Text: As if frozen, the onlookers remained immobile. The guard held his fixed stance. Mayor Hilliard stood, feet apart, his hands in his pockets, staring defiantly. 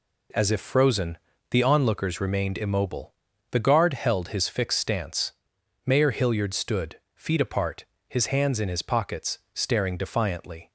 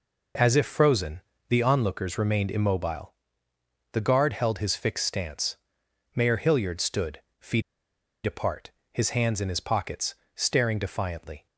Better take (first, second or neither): first